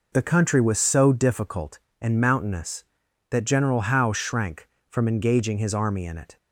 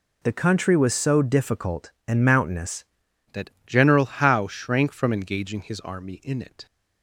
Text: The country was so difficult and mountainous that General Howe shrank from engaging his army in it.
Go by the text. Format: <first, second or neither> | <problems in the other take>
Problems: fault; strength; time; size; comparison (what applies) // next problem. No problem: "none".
first | changes voice at "that"; from 3.3 s on; 3.3 s long // pauses between "that" and "General"; slight; at 3.4 s; 0.16 s long